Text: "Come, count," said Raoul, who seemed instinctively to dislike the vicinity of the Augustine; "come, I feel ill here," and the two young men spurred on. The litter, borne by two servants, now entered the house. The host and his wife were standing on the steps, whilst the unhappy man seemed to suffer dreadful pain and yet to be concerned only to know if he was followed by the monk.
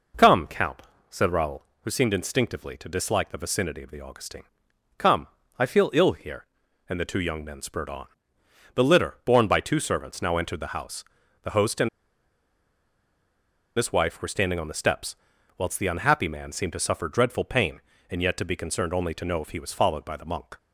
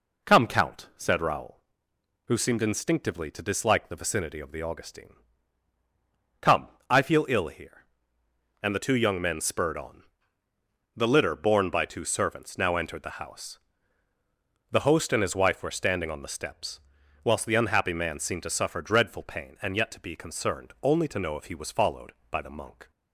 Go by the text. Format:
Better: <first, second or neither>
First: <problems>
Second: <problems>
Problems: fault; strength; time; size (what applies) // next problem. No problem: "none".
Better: second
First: pauses between "and" and "his"; strong; at 11.8 s; 1.8 s long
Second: none